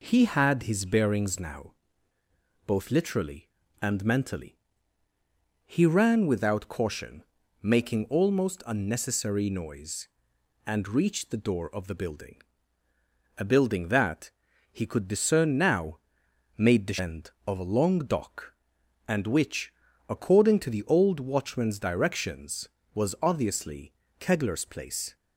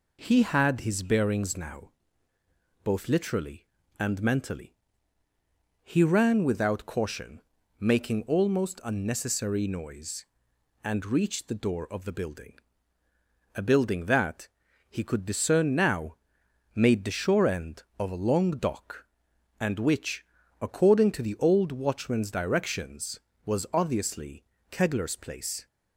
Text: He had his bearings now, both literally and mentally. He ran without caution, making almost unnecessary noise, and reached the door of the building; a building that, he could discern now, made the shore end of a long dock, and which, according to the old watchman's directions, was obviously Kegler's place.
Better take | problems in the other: second | skips "shore"; at 16.9 s // pauses between "obviously" and "Kegler's"; slight; at 23.9 s; 0.26 s long; slight in the second

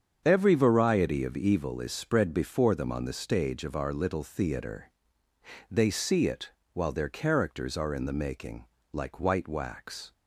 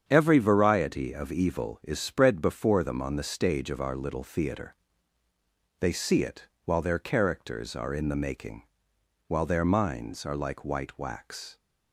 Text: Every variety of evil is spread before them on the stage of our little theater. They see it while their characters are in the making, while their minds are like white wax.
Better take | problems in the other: second | starts louder than the rest; strong; until 1.2 s; 7.5 dB; strong in the second // pauses between "it" and "while"; slight; at 6.5 s; 0.22 s long; slight in the second // skips "while their minds are"; at 8.7 s

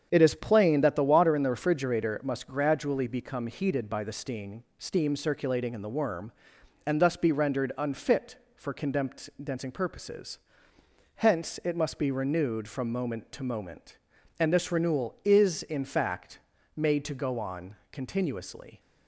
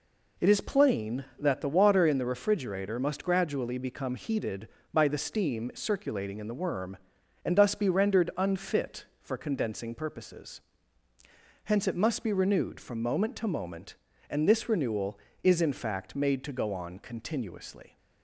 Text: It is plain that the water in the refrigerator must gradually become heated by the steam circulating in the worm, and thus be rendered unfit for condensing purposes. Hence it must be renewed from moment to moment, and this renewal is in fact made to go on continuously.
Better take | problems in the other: second | starts louder than the rest; strong; until 1.1 s; 7.5 dB // says "steam" twice; at 4.7 s // pauses between "fact" and "made"; slight; at 16.3 s; 0.36 s long // pauses between "on" and "continuously"; slight; at 17.7 s; 0.16 s long

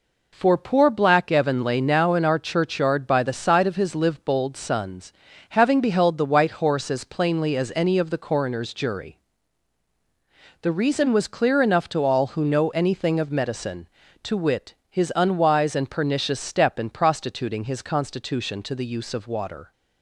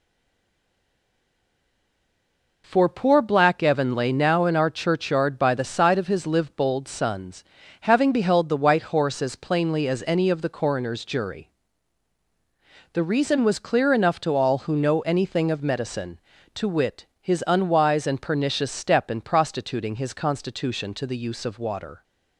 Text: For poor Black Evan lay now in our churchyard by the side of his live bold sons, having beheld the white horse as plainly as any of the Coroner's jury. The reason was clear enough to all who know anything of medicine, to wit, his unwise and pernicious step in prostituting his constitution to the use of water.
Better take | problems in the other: first | stays silent before the first word; strong; until 2.6 s; 2.6 s long

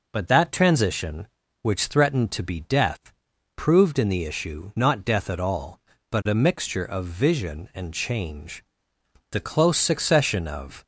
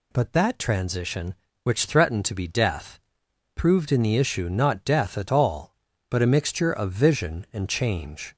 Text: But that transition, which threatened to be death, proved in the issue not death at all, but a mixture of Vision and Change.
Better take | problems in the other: second | goes on to say "The close succession of"; from 9.2 s on; 1.5 s long

